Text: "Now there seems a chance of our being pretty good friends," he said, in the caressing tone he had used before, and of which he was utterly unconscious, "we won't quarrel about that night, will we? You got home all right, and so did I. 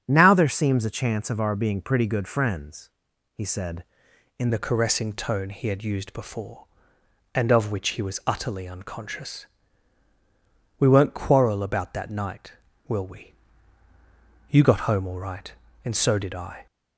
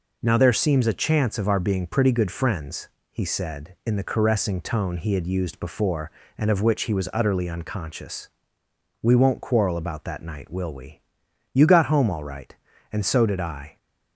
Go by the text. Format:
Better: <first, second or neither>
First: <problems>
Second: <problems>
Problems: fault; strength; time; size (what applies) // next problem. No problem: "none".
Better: second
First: starts louder than the rest; strong; until 1.0 s; 7.5 dB // changes voice at "the"; from 4.4 s on; 12.2 s long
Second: none